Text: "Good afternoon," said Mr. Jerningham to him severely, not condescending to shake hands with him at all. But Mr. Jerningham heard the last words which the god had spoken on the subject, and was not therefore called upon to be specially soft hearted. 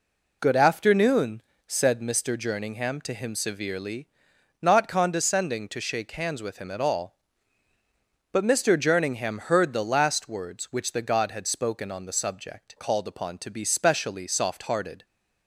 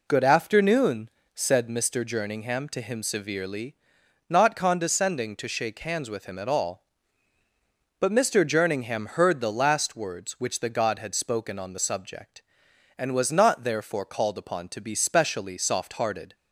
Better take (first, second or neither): second